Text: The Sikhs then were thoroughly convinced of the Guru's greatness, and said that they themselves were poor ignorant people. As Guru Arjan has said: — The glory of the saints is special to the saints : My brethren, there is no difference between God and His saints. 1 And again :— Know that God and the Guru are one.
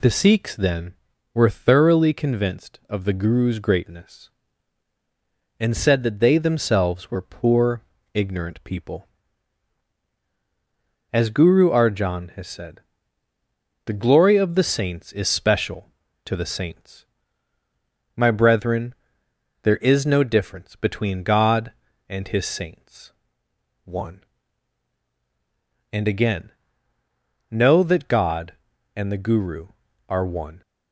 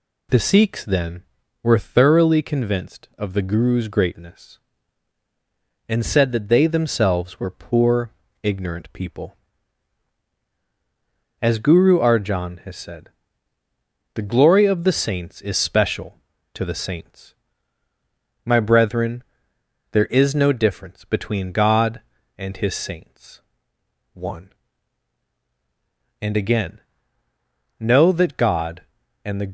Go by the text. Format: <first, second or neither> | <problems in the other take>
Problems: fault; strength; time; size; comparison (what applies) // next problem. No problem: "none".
first | pauses between "poor" and "ignorant"; slight; at 8.1 s; 0.32 s long; slight in the first // stops before "Guru are one"; at 29.4 s